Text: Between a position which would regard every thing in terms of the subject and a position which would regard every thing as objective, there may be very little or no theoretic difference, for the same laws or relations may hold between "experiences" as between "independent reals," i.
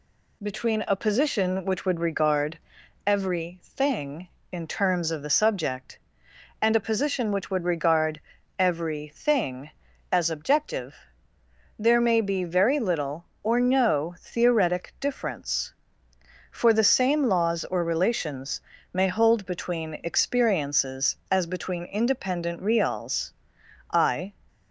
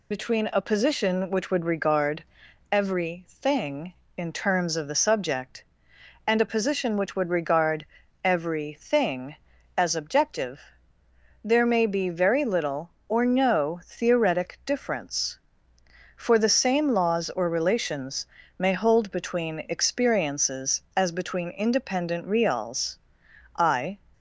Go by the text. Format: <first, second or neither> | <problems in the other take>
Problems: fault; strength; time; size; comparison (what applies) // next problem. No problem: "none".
first | loses the start of "Between"; at 0.1 s; 40 ms // pauses between "regard" and "every"; noticeable; at 2.2 s; 0.48 s long; noticeable in the first // pauses between "regard" and "every"; at 7.8 s; 0.38 s long; also in the first // pauses between "relations" and "may"; slight; at 18.2 s; 0.32 s long; slight in the first